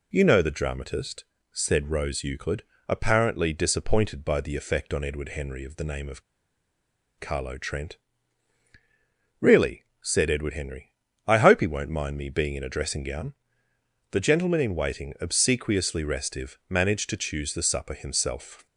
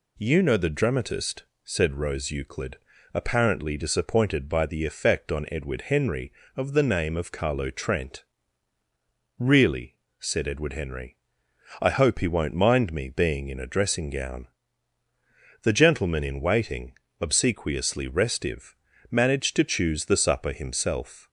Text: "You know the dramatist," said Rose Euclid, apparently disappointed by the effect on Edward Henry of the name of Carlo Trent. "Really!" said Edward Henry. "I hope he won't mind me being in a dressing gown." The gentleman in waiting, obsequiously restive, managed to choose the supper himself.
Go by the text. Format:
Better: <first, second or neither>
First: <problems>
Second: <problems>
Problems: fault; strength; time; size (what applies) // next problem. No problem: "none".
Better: second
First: pauses between "of" and "Carlo"; noticeable; at 6.2 s; 0.96 s long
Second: none